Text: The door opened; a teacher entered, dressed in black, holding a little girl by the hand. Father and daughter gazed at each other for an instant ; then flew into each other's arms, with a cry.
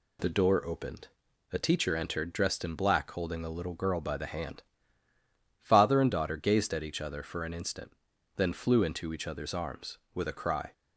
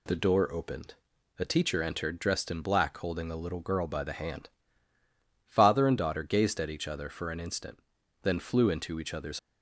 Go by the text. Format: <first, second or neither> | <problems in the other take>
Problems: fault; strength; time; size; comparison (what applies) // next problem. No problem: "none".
first | stops before "arms with a cry"; at 9.3 s